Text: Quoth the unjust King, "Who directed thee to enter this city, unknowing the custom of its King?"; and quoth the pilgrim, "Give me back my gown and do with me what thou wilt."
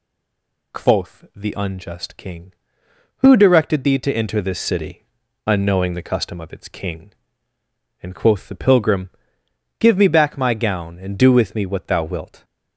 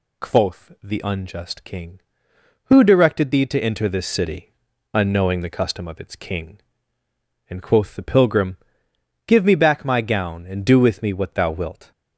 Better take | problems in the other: second | stays silent before the first word; slight; until 0.7 s; 0.7 s long

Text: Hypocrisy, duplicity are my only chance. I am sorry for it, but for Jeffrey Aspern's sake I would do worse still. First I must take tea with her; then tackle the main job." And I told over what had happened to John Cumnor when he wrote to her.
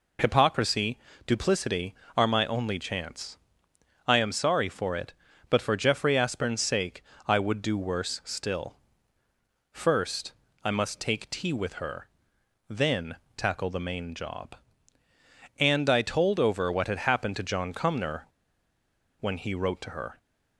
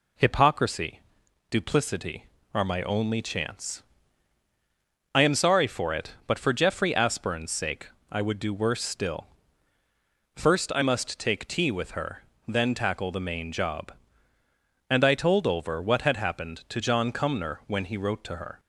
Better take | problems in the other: second | pauses between "sake" and "I"; slight; at 7.0 s; 0.24 s long; slight in the second // pauses between "First" and "I"; slight; at 10.3 s; 0.30 s long // pauses between "then" and "tackle"; slight; at 13.1 s; 0.22 s long // pauses between "Cumnor" and "when"; noticeable; at 18.2 s; 0.95 s long

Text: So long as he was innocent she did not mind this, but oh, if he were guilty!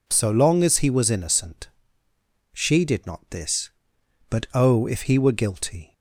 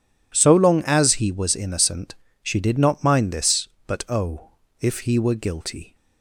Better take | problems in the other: second | pauses between "innocent" and "she"; noticeable; at 1.6 s; 0.84 s long; slight in the second // skips "mind"; at 3.2 s

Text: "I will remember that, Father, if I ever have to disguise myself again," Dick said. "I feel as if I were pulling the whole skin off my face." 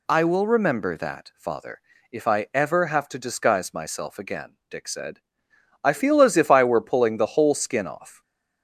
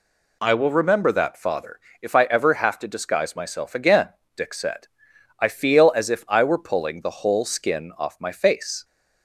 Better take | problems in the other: second | stops before "my face"; at 8.2 s

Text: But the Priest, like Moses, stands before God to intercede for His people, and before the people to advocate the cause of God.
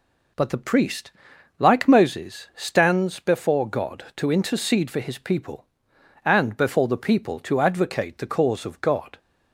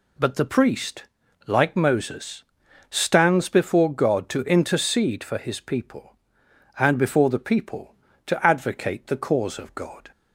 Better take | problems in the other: neither | none

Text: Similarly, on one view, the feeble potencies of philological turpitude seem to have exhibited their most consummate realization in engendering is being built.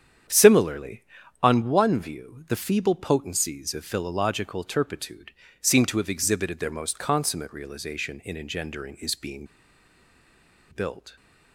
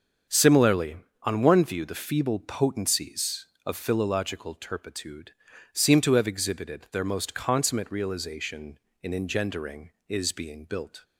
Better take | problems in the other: second | starts louder than the rest; strong; until 1.6 s; 8.5 dB; strong in the second // pauses between "turpitude" and "seem"; slight; at 5.3 s; 0.30 s long; also in the second // pauses between "being" and "built"; strong; at 9.4 s; 1.2 s long

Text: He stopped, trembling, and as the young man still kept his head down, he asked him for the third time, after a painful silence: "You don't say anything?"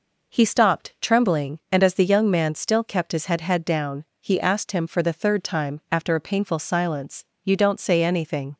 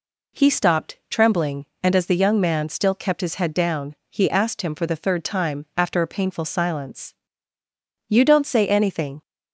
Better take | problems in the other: second | says "head" twice; at 3.4 s

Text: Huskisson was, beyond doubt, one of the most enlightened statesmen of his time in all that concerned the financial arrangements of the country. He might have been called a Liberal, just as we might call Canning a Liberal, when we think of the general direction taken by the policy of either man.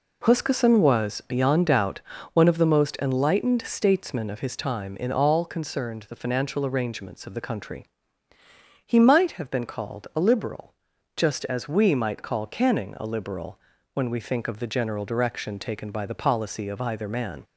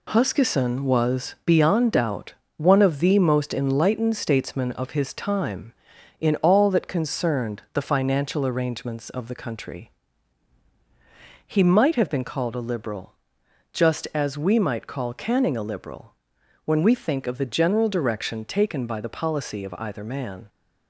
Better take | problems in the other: second | skips "that"; at 5.4 s

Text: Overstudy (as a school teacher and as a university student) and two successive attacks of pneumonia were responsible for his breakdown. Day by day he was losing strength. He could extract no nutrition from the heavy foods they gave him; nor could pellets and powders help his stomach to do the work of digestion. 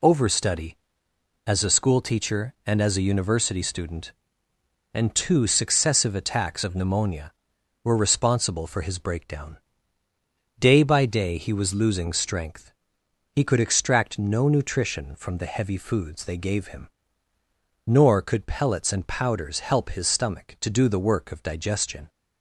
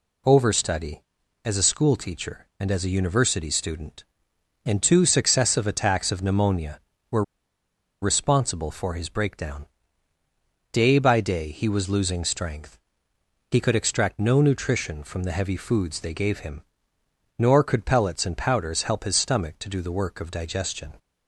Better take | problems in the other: first | pauses between "were" and "responsible"; noticeable; at 7.2 s; 0.80 s long

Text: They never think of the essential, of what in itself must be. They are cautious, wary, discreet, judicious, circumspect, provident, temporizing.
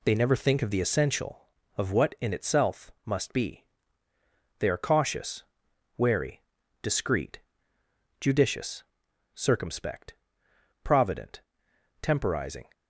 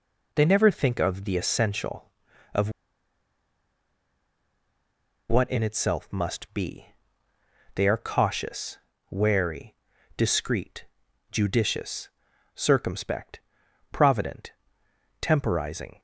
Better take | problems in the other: first | pauses between "of" and "what"; strong; at 2.6 s; 2.5 s long

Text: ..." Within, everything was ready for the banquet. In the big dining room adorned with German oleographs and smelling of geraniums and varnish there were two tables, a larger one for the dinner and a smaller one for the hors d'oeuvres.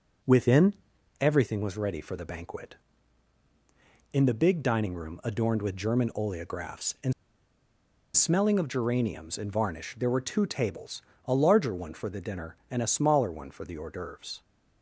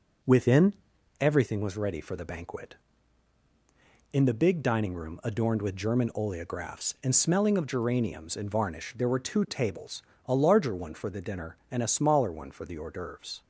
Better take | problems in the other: second | pauses between "and" and "smelling"; at 7.1 s; 1.0 s long

